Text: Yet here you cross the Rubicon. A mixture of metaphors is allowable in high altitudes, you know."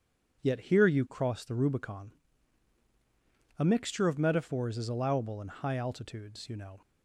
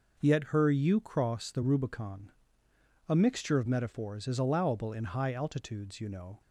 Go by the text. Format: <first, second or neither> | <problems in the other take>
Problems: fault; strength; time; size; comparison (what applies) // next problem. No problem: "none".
first | says "her" for "here"; at 0.4 s